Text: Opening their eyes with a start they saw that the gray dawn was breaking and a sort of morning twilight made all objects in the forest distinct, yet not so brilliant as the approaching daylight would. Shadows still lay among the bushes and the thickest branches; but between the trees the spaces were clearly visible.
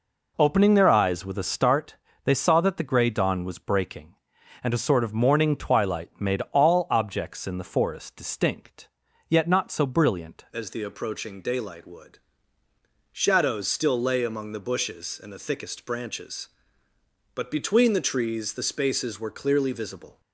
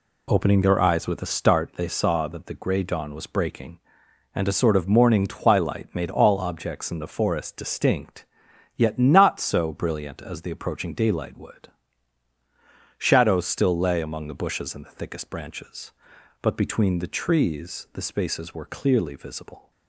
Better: second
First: pauses between "start" and "they"; slight; at 1.9 s; 0.28 s long // changes voice at "as"; from 10.5 s on; 9.7 s long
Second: none

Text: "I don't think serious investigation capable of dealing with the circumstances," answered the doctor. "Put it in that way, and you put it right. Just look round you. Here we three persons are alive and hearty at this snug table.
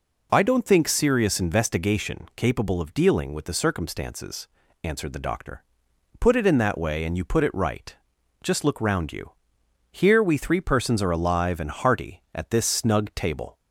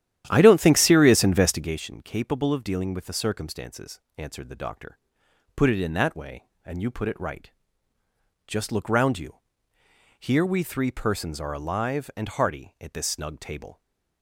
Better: first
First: none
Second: starts louder than the rest; strong; until 1.8 s; 11.5 dB // stays silent after the last word; slight; from 13.7 s on; 0.5 s long

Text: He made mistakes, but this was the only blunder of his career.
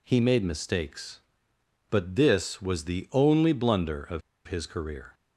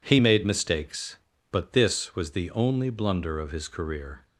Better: second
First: pauses between "of" and "his"; slight; at 4.2 s; 0.26 s long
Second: none

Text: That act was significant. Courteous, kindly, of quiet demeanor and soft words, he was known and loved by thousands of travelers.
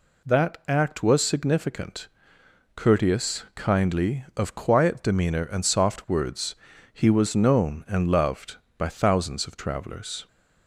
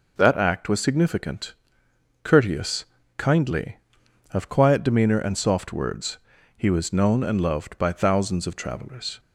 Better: neither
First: none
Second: none

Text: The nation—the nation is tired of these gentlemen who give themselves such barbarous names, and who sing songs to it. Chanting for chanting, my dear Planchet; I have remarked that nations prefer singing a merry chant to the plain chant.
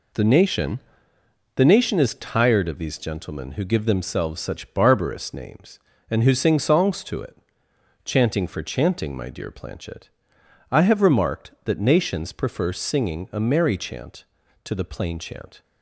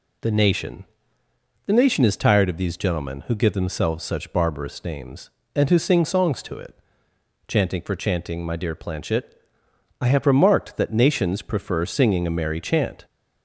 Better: first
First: none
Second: stops before "to the plain chant"; at 13.0 s

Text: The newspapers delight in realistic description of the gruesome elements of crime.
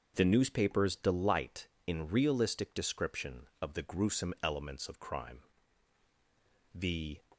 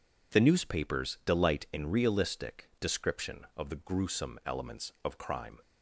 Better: second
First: starts louder than the rest; until 1.1 s; 6.5 dB // goes on to say "The"; slight; from 6.7 s on; 0.46 s long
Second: none

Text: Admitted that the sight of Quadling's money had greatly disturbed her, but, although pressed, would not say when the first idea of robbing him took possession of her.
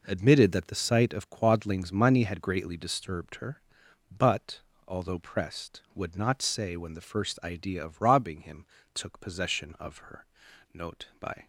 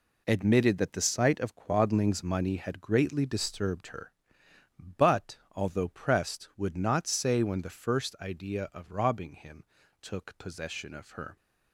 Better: second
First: pauses between "him" and "took"; slight; at 8.6 s; 0.28 s long // goes on to say "Note by"; noticeable; from 10.7 s on; 0.72 s long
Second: pauses between "him" and "took"; slight; at 9.6 s; 0.36 s long

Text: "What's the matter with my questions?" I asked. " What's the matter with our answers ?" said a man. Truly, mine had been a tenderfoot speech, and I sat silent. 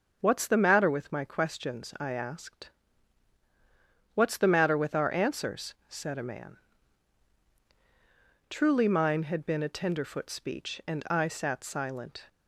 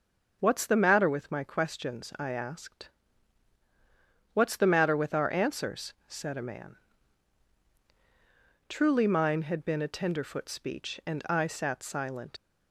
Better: first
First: none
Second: leaves "silent" unfinished; at 12.3 s; 105 ms

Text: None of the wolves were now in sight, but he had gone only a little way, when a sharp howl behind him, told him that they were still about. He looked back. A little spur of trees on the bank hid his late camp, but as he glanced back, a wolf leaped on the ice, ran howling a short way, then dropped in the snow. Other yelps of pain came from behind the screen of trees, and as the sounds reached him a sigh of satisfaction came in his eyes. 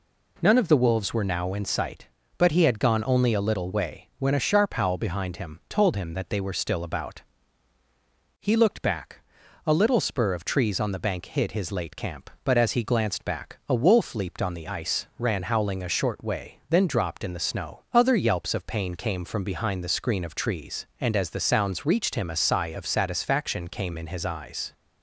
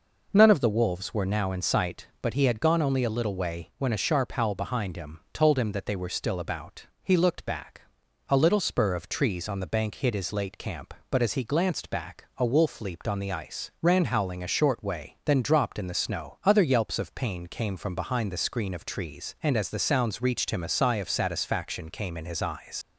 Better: first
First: none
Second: leaves "eyes" unfinished; at 22.8 s; 105 ms

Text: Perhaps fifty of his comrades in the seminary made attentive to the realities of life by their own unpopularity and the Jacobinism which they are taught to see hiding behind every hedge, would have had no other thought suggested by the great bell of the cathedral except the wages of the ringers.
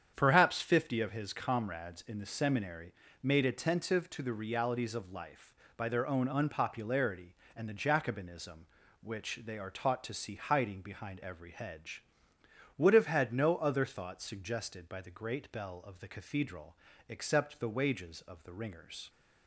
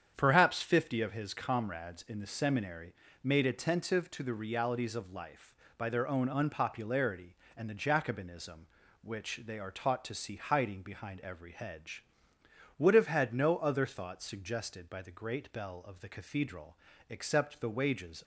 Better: first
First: starts louder than the rest; strong; until 1.1 s; 8.5 dB // pauses between "seminary" and "made"; slight; at 2.9 s; 0.30 s long // pauses between "cathedral" and "except"; slight; at 16.7 s; 0.34 s long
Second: starts louder than the rest; strong; until 1.1 s; 8 dB // pauses between "seminary" and "made"; slight; at 2.9 s; 0.30 s long // pauses between "cathedral" and "except"; slight; at 16.7 s; 0.34 s long // stops before "of the ringers"; at 18.2 s

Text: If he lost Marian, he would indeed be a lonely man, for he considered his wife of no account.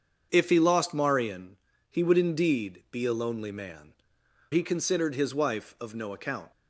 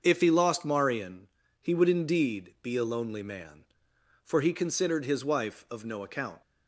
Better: second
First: starts louder than the rest; until 1.3 s; 7 dB // skips "for"; at 4.2 s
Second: starts louder than the rest; until 1.0 s; 6.5 dB

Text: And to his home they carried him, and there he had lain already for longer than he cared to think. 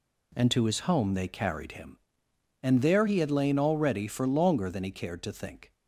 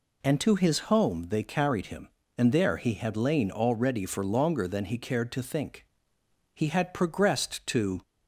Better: first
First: none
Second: goes on to say "He had progressed to"; from 6.5 s on; 1.4 s long

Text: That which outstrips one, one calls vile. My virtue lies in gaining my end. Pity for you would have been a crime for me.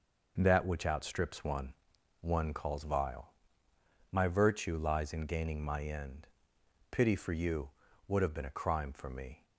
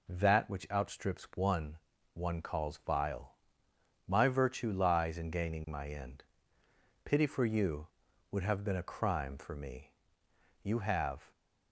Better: first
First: none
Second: goes on to say "You have"; noticeable; from 10.6 s on; 0.68 s long

